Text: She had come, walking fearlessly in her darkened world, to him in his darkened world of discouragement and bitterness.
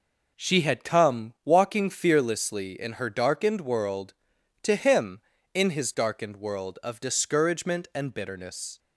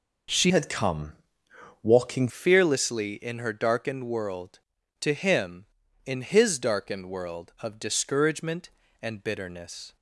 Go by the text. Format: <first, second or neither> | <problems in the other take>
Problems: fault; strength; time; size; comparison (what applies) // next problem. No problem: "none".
first | changes voice from "had" to "walking"; from 0.4 to 2.2 s; 1.8 s long